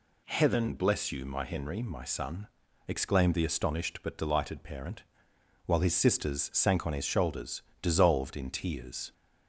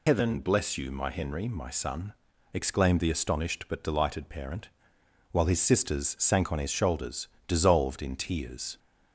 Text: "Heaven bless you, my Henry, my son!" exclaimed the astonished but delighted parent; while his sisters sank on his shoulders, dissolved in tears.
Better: first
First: none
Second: loses the start of "Heaven"; at 0.0 s; 165 ms

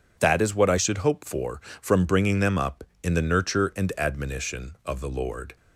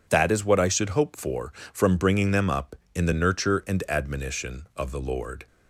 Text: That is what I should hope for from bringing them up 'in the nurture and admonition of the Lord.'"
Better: neither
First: none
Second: none

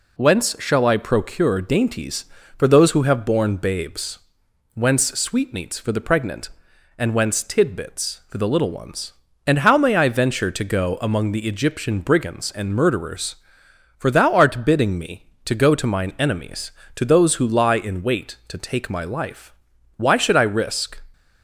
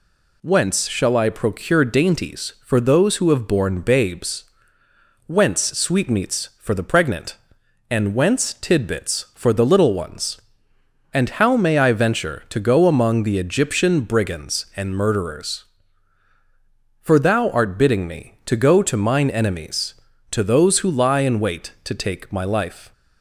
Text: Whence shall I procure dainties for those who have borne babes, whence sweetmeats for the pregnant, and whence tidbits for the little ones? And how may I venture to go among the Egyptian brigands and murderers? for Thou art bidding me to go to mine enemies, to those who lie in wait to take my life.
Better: second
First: goes on to say "Why should I risk"; noticeable; from 19.9 s on; 1.0 s long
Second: none

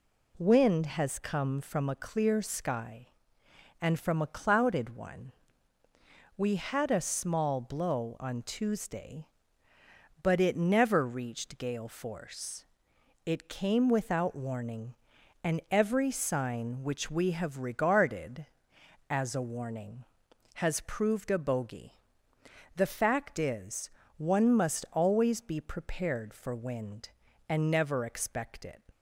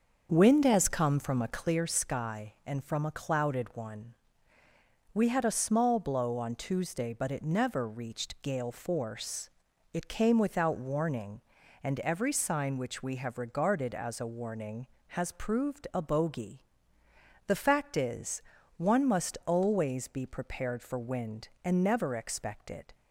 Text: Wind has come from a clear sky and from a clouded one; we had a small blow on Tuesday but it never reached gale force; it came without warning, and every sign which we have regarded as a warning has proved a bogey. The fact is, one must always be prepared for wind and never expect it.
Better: first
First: none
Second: starts louder than the rest; until 2.0 s; 6.5 dB

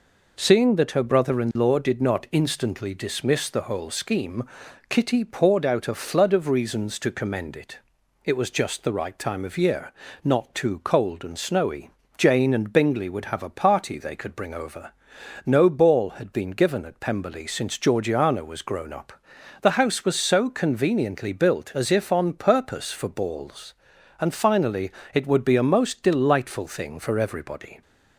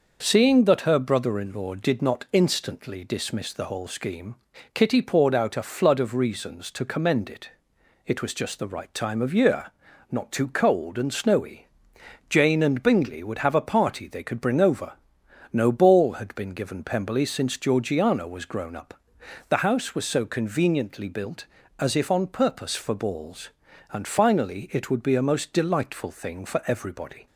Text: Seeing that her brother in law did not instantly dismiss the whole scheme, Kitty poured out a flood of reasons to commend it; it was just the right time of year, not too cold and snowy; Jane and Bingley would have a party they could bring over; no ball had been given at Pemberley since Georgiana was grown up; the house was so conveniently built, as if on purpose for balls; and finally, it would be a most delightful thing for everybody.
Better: first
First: none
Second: starts louder than the rest; noticeable; until 1.2 s; 6 dB // skips "at"; at 16.8 s

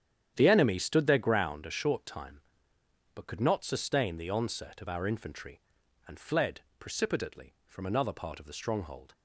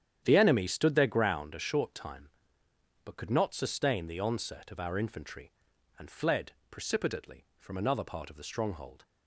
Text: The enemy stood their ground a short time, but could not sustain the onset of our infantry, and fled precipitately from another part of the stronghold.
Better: neither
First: starts louder than the rest; strong; until 1.3 s; 9.5 dB // pauses between "fled" and "precipitately"; slight; at 6.6 s; 0.18 s long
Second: starts louder than the rest; strong; until 1.2 s; 9.5 dB // pauses between "fled" and "precipitately"; slight; at 6.5 s; 0.18 s long

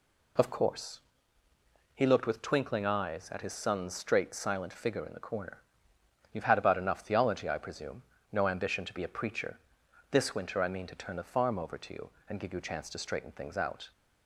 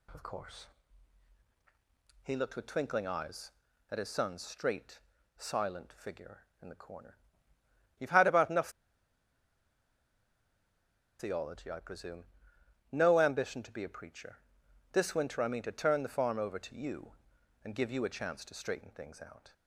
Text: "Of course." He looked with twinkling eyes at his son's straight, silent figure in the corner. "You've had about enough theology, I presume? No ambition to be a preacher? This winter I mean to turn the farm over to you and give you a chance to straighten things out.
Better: first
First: none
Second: pauses between "enough" and "theology"; strong; at 8.6 s; 2.4 s long

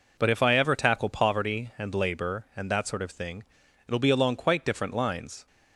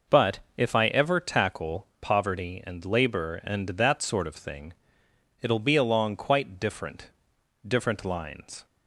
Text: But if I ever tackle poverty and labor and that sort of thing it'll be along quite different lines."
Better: first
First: pauses between "thing" and "it'll"; at 3.4 s; 0.42 s long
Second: pauses between "But" and "if"; slight; at 0.3 s; 0.16 s long // pauses between "thing" and "it'll"; noticeable; at 4.7 s; 0.68 s long // says "different" twice; at 7.6 s

